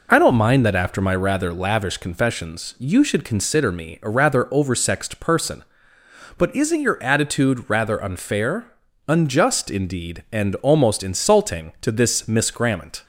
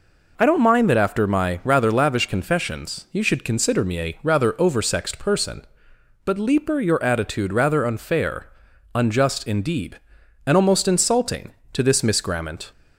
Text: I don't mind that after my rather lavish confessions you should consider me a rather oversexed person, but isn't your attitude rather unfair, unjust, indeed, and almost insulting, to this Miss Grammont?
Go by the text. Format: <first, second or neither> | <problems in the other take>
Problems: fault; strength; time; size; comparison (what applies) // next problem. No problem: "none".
first | says "leaper" for "isn't"; at 6.3 s